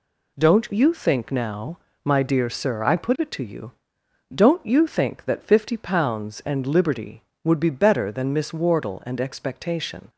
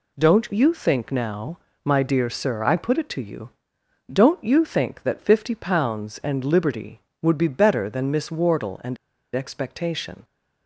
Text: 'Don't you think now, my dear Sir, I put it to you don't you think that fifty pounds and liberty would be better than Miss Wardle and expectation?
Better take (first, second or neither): first